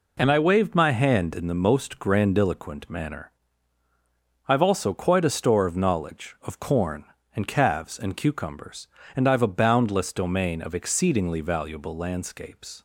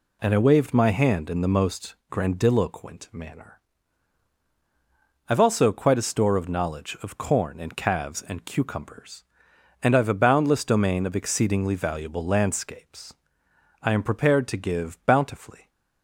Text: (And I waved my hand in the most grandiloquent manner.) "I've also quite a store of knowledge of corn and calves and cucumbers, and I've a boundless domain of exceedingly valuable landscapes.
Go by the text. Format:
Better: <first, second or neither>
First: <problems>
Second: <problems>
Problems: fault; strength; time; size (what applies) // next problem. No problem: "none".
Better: first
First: none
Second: goes on to say "I am prepared to give bountifully"; strong; from 13.8 s on; 1.8 s long